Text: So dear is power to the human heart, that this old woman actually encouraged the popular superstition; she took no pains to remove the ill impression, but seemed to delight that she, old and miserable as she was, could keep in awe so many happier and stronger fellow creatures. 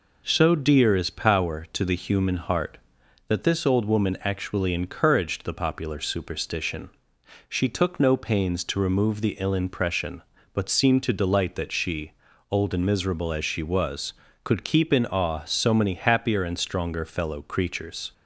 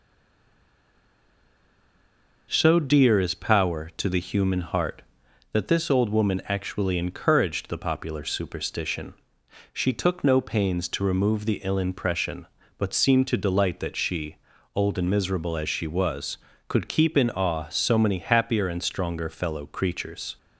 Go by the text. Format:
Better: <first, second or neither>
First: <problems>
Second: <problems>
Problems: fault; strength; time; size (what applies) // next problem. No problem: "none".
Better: first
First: none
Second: stays silent before the first word; until 2.4 s; 2.4 s long